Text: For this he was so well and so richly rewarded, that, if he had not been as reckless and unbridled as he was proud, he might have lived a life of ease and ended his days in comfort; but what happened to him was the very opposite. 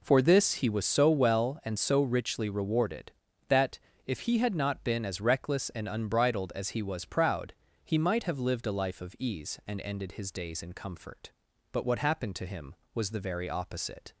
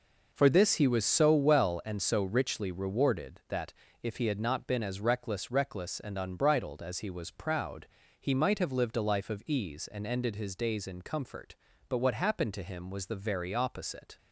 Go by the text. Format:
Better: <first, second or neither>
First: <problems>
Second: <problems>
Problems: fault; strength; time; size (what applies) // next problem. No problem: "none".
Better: first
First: none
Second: says "reckless" twice; at 5.5 s